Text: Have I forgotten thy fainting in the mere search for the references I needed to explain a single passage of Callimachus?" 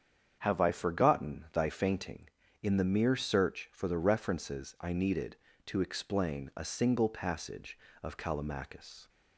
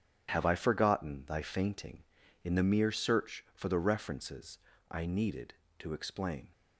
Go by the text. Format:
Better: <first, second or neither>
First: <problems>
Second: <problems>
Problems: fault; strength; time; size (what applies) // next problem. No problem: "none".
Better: first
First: starts louder than the rest; strong; until 1.4 s; 8 dB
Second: starts louder than the rest; strong; until 1.3 s; 8.5 dB // pauses between "references" and "I"; slight; at 4.5 s; 0.32 s long // stops before "a single passage of Callimachus"; at 6.5 s